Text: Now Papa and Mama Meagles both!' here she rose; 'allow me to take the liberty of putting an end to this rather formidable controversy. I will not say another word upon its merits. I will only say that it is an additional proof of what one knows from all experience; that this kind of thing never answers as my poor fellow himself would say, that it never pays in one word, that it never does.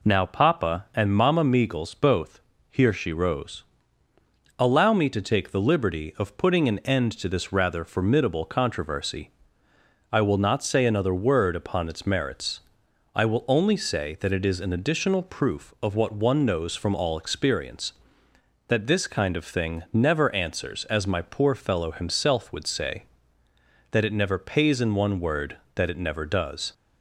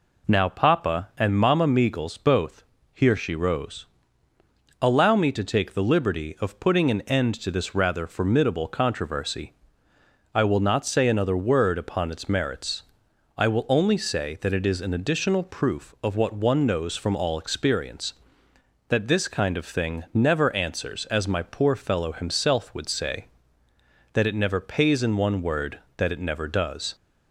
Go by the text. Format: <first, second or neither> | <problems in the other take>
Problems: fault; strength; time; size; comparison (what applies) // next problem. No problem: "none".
neither | none